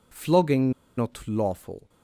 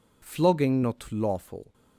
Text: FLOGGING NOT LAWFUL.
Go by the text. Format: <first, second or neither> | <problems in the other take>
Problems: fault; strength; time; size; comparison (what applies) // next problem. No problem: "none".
second | pauses between "FLOGGING" and "NOT"; slight; at 0.7 s; 0.27 s long